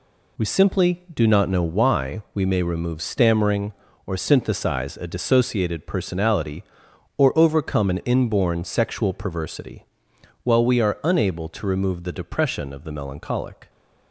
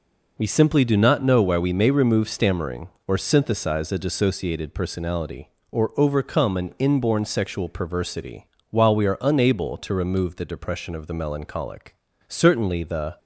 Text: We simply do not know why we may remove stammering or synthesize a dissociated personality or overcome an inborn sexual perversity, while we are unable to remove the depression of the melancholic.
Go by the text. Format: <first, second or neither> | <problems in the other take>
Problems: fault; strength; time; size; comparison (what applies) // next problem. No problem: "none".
first | goes on to say "Certainly the"; noticeable; from 12.2 s on; 0.90 s long